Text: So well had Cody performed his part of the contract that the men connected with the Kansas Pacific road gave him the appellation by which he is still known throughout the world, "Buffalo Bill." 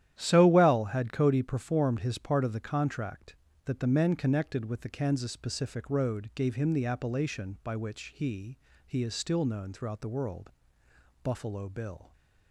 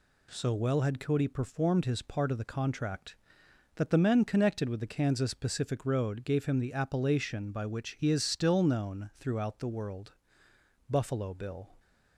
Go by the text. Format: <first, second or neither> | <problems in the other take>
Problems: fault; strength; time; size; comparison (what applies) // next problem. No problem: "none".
second | starts louder than the rest; strong; until 1.1 s; 11.5 dB // says "he" twice; at 8.8 s